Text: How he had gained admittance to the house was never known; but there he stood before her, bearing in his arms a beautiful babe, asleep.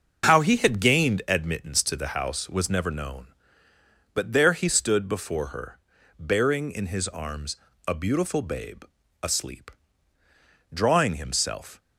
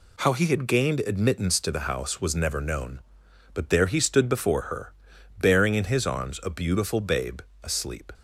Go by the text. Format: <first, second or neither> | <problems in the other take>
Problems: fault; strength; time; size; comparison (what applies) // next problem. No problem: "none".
second | pauses between "arms" and "a"; slight; at 7.5 s; 0.30 s long // goes on to say "Drawing himself"; noticeable; from 10.7 s on; 1.0 s long